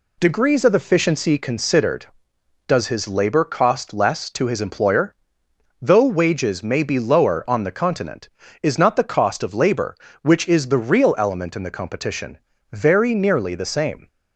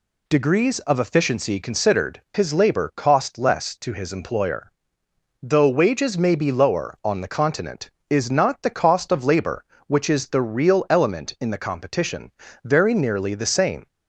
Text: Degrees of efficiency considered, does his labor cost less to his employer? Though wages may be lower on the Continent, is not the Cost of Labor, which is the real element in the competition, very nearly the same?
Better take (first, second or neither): first